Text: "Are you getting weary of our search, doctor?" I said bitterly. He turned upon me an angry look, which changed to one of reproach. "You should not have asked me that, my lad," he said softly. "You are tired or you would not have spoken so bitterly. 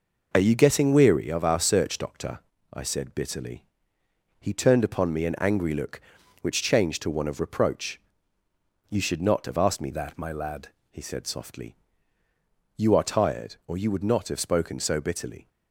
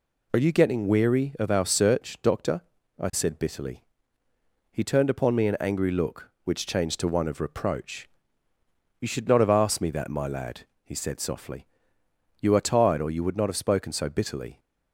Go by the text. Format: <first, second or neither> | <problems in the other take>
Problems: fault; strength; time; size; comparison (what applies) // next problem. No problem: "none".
second | changes voice from "that" to "lad"; from 9.9 to 10.6 s; 0.7 s long